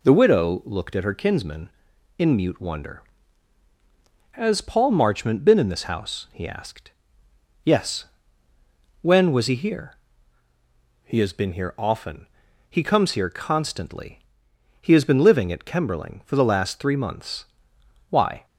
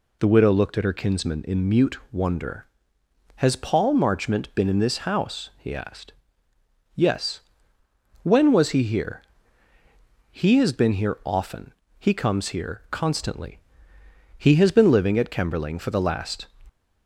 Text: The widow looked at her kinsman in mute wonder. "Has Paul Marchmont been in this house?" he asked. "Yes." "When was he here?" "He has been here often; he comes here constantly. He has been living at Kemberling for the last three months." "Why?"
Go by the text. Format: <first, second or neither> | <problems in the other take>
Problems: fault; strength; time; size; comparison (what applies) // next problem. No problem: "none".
first | stops before "three months Why"; at 16.6 s